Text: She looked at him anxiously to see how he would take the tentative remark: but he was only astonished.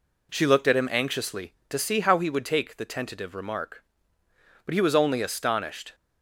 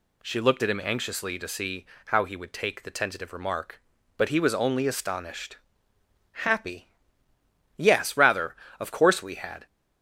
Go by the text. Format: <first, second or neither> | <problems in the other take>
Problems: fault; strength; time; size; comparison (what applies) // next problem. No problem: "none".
first | pauses between "see" and "how"; slight; at 1.8 s; 0.20 s long // goes on to say "Happy Yes rather Of course we had"; strong; from 6.3 s on; 3.3 s long